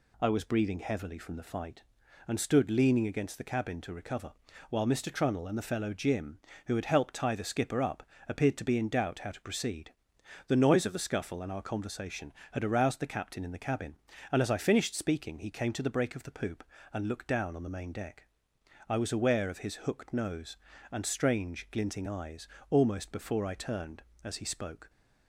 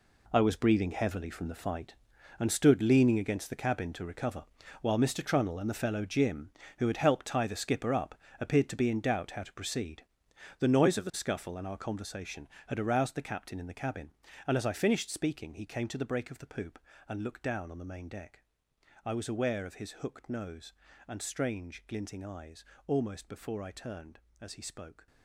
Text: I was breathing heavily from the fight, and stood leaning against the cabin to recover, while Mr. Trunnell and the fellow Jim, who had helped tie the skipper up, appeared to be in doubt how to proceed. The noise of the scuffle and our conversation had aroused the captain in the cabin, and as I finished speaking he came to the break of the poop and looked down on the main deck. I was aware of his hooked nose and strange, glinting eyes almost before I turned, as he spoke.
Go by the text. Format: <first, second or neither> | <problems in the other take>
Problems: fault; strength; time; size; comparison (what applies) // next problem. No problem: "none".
first | gets quieter; strong; throughout; 12.5 dB // pauses between "eyes" and "almost"; slight; at 22.6 s; 0.22 s long; slight in the first